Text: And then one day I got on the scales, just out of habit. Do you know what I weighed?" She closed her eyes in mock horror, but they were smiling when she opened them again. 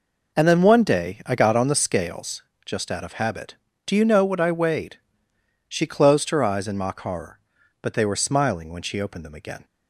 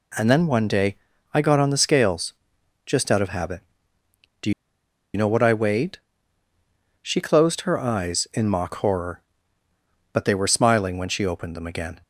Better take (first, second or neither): first